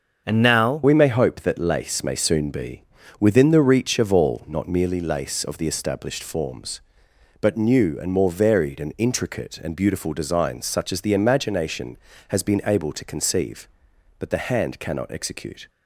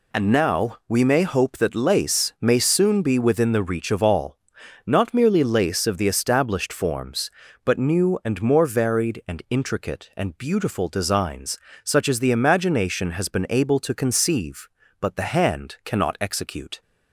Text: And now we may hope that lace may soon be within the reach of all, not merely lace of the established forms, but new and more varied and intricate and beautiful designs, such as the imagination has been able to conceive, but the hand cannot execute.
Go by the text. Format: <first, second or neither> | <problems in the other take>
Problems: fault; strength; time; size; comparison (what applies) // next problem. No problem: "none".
second | starts louder than the rest; until 1.2 s; 6.5 dB // changes voice at "we"; from 0.8 s on; 14.8 s long // pauses between "be" and "within"; at 2.8 s; 0.38 s long